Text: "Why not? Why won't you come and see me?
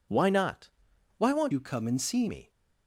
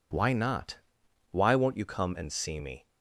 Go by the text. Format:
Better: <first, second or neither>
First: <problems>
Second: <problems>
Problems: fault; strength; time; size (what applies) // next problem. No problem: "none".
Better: second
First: changes voice from "you" to "see"; from 1.5 to 2.2 s; 0.7 s long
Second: none